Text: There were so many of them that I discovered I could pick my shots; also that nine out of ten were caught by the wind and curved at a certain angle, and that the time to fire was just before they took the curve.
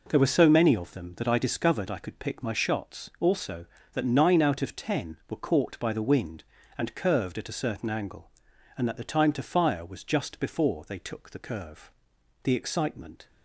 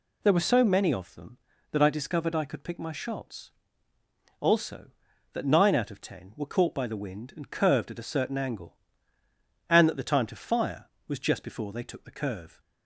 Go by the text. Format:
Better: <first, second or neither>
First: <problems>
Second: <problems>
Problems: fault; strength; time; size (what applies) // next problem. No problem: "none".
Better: second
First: goes on to say "The excitement"; noticeable; from 12.4 s on; 0.82 s long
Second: none